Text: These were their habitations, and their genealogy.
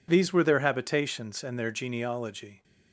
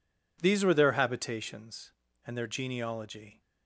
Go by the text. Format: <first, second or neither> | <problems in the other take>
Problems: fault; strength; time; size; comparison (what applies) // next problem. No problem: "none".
neither | none